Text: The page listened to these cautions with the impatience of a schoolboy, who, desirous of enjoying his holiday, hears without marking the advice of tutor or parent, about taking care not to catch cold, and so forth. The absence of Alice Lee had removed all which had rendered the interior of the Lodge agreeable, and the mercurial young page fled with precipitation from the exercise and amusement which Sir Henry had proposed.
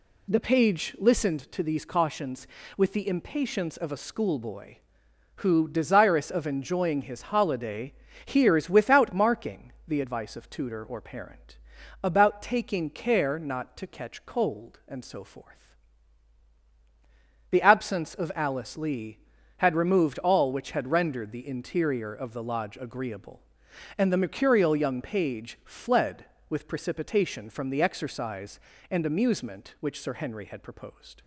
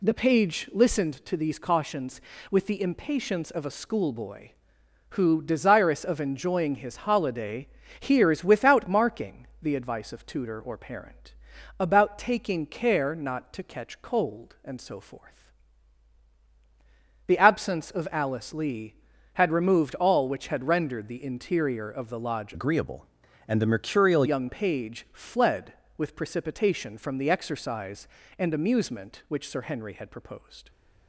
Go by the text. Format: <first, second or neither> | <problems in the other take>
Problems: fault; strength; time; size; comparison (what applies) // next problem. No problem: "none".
first | pauses between "marking" and "the"; slight; at 9.4 s; 0.16 s long; slight in the first // changes voice from "agreeable" to "mercurial"; from 22.5 to 24.2 s; 1.7 s long